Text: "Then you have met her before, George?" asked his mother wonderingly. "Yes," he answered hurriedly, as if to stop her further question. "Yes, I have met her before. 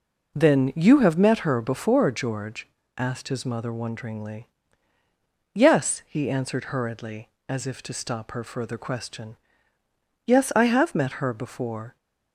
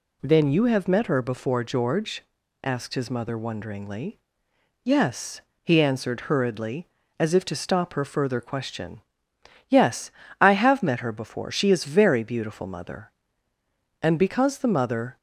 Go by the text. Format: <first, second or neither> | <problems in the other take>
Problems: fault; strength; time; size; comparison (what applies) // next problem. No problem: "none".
first | goes on to say "She is very beautiful mother And because the mother"; strong; from 11.5 s on; 3.6 s long